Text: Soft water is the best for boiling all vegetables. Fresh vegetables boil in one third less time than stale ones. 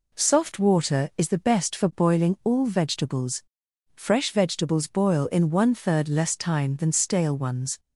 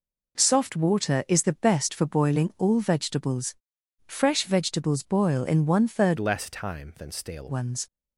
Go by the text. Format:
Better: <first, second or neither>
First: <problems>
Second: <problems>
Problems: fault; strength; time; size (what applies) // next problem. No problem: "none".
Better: first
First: none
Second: changes voice from "less" to "stale"; from 6.1 to 7.4 s; 1.3 s long